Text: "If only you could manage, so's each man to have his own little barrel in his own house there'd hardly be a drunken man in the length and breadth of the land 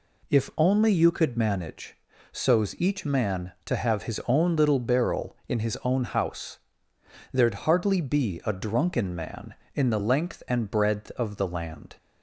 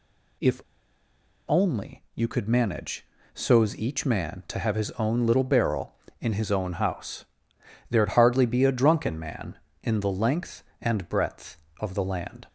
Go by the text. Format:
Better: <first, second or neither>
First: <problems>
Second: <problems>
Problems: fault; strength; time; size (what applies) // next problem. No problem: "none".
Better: first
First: pauses between "house" and "there'd"; noticeable; at 6.5 s; 0.75 s long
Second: pauses between "If" and "only"; noticeable; at 0.6 s; 0.88 s long // pauses between "house" and "there'd"; noticeable; at 7.2 s; 0.66 s long